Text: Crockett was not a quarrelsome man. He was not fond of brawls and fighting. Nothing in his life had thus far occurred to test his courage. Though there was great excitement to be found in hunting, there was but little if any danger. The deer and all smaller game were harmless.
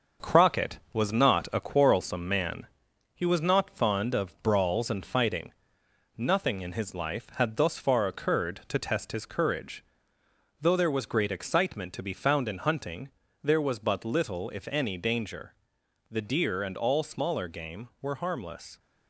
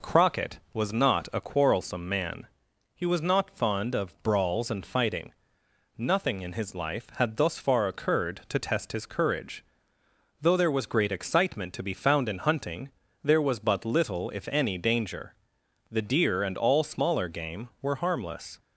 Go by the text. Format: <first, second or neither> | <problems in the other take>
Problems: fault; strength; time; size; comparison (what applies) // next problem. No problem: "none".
second | gets quieter; noticeable; throughout; 4.5 dB